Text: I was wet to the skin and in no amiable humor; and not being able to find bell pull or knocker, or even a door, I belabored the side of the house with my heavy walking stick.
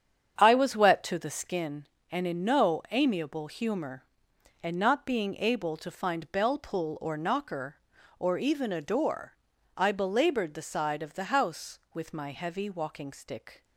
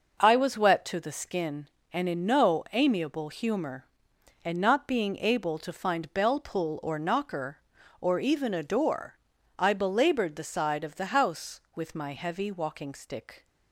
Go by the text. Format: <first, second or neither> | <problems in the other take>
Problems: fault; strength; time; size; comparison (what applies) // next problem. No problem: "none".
second | starts louder than the rest; strong; until 1.6 s; 8 dB